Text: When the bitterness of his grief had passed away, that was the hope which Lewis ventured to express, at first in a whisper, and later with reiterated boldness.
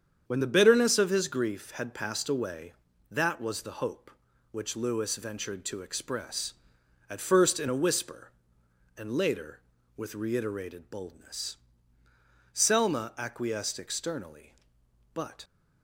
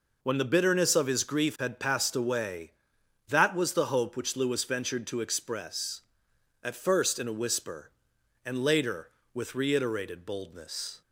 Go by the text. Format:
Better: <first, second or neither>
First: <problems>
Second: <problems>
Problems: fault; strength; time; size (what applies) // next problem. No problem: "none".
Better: second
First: starts louder than the rest; strong; until 1.2 s; 8 dB // goes on to say "Selma acquiesced externally but"; strong; from 12.5 s on; 2.9 s long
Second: none